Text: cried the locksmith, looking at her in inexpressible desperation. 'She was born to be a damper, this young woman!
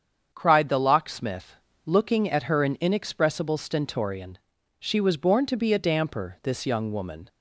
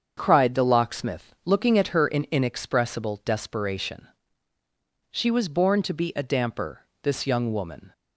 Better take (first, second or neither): second